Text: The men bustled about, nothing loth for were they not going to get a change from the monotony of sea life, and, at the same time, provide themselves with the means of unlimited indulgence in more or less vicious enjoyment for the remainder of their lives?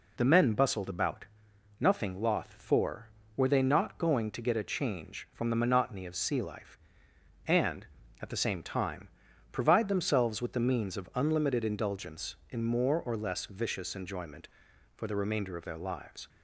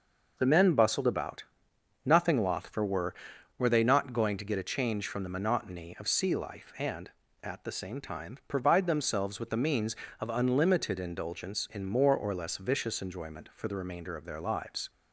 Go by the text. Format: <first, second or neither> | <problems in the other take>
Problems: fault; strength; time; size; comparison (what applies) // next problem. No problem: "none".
first | says "were" twice; at 3.5 s